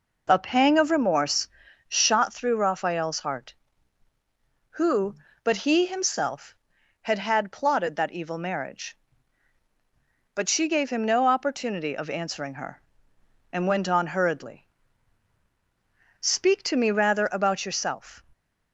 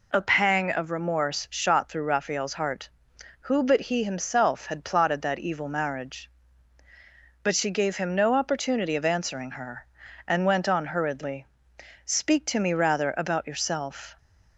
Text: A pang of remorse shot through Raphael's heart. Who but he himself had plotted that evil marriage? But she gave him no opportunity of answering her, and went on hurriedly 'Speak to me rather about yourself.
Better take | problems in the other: second | pauses between "remorse" and "shot"; at 1.4 s; 0.40 s long // says "had" twice; at 7.1 s // pauses between "hurriedly" and "Speak"; strong; at 14.6 s; 1.5 s long; noticeable in the second

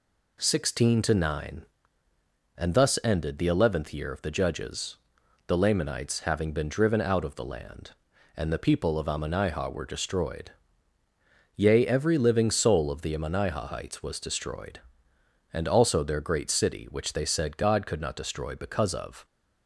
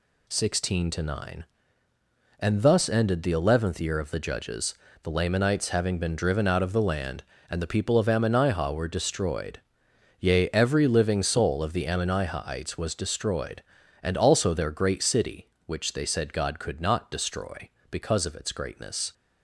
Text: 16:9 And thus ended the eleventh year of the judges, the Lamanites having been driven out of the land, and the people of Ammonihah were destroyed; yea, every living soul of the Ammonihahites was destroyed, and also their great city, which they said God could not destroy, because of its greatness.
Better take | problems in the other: second | stops before "its greatness"; at 19.2 s

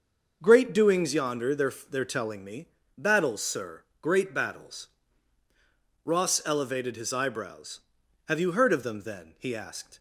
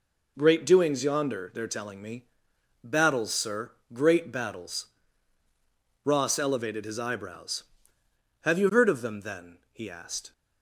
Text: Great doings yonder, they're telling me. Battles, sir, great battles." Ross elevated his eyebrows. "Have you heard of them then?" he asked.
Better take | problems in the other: second | says "they're" twice; at 1.8 s

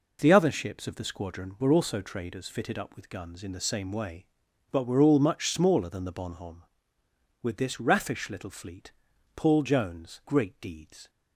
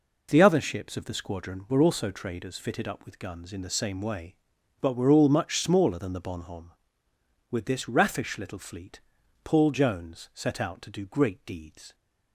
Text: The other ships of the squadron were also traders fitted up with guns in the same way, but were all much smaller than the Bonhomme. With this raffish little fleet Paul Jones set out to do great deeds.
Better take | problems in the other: second | pauses between "fleet" and "Paul"; at 8.9 s; 0.42 s long; also in the second // skips "set out to do"; at 10.2 s

